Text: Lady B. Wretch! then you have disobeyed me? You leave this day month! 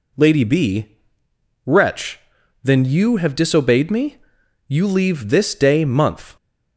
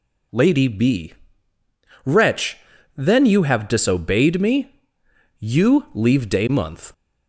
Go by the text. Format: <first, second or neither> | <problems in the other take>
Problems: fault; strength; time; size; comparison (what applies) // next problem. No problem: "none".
first | skips "this"; at 6.2 s